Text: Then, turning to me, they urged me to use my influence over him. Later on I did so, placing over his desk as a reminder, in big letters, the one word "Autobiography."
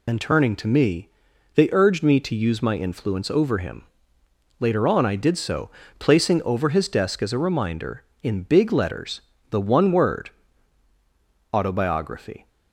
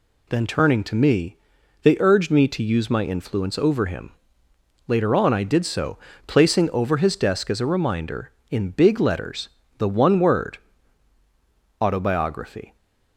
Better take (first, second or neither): second